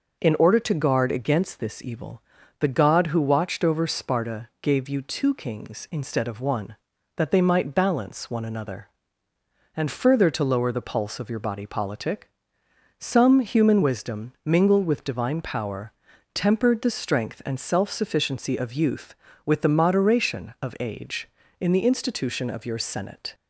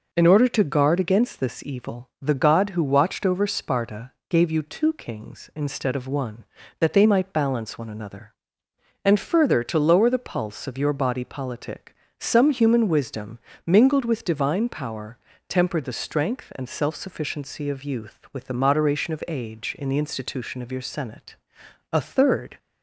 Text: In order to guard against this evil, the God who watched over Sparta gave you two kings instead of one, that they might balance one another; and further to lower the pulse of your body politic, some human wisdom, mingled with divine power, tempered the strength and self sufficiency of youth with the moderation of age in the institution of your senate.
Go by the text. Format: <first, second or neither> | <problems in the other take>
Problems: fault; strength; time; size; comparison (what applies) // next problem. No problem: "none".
first | pauses between "Sparta" and "gave"; slight; at 4.1 s; 0.18 s long // goes on to say "A third"; noticeable; from 21.9 s on; 0.66 s long